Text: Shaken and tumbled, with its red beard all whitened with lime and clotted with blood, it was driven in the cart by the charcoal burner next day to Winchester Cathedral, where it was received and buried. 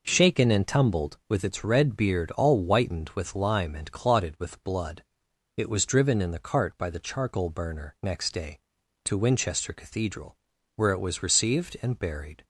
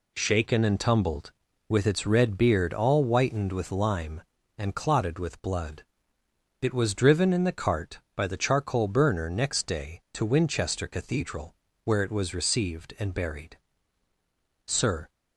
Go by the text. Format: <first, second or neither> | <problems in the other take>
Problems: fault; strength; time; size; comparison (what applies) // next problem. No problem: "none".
first | goes on to say "Sir"; slight; from 14.6 s on; 0.42 s long